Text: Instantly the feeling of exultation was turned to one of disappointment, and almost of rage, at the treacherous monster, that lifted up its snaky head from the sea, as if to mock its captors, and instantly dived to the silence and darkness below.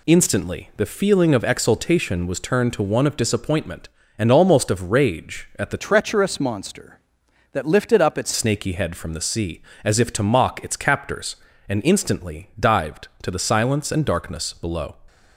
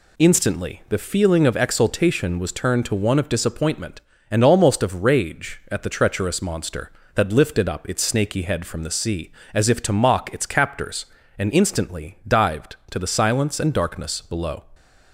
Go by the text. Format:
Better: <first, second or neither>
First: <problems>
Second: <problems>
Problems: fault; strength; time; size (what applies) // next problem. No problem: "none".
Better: second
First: changes voice from "treacherous" to "its"; from 5.7 to 8.3 s; 2.6 s long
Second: none